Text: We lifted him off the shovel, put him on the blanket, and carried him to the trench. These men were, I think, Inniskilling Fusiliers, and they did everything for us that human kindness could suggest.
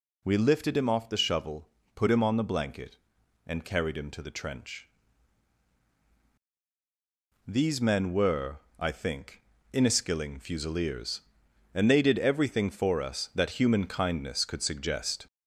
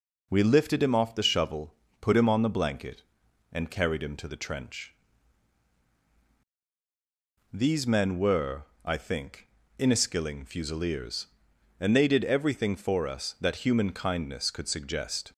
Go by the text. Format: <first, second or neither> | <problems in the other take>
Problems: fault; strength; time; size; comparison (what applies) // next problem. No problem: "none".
second | gets louder; slight; throughout; 2 dB